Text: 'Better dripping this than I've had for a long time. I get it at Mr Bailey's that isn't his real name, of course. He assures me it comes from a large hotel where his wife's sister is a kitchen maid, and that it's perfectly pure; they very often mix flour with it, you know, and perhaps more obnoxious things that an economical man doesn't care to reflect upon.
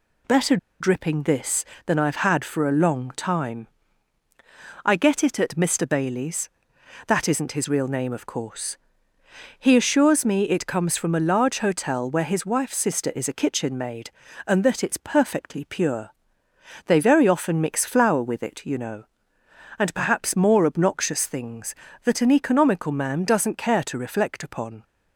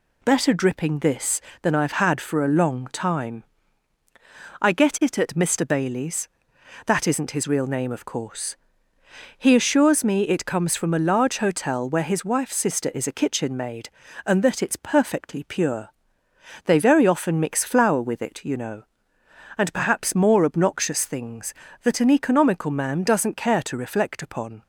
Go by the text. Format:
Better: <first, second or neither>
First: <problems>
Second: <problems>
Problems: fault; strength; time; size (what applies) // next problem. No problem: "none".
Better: second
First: pauses between "Better" and "dripping"; slight; at 0.5 s; 0.23 s long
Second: none